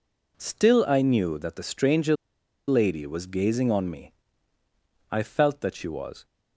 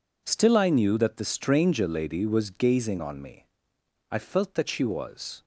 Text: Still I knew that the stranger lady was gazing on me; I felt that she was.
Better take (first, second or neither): second